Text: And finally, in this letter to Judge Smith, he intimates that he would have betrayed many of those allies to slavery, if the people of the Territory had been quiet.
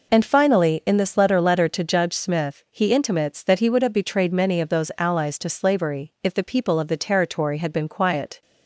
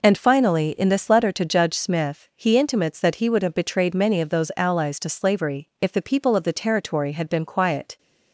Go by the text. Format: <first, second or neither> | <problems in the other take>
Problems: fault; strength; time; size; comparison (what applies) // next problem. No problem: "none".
second | says "letter" twice; at 1.3 s